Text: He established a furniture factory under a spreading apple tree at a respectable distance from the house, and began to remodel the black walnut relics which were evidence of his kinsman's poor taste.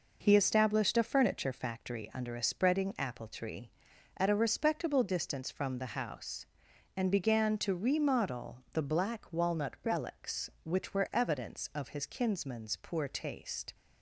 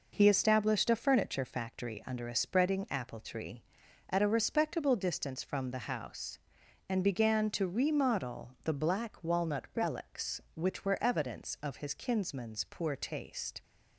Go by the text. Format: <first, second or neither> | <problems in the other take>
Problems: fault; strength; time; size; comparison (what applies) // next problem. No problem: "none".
neither | none